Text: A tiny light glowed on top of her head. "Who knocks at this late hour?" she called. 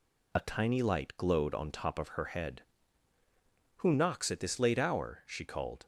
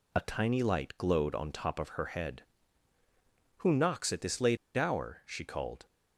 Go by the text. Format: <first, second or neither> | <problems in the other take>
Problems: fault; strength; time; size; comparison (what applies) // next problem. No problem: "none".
first | pauses between "late" and "hour"; slight; at 4.5 s; 0.20 s long